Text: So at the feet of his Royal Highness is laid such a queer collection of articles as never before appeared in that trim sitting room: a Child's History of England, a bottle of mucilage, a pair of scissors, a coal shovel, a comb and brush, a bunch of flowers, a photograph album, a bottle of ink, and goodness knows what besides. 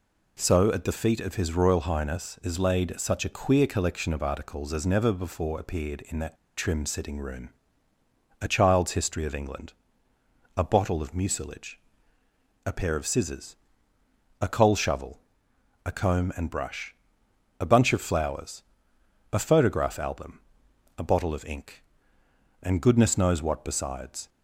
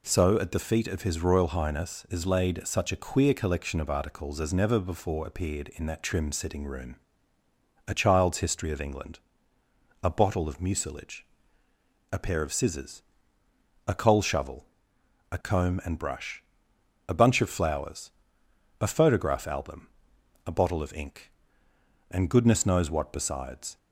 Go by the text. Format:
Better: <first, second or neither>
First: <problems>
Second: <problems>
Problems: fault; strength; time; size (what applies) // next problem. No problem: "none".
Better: second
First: pauses between "that" and "trim"; slight; at 6.3 s; 0.21 s long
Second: none